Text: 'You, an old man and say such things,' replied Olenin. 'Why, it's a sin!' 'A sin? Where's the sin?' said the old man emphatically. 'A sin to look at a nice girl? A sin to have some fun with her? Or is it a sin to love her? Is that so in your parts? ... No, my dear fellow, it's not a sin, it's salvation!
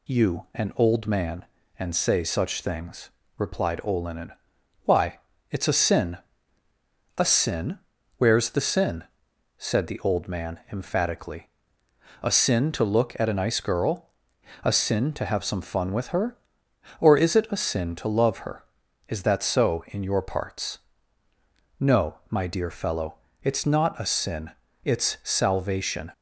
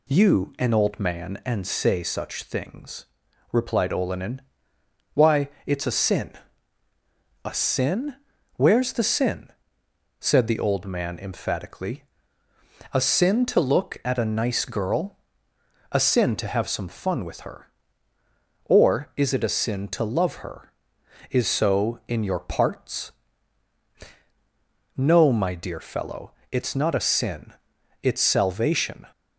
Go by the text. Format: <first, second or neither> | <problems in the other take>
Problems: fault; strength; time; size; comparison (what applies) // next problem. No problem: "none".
first | skips "that"; at 21.4 s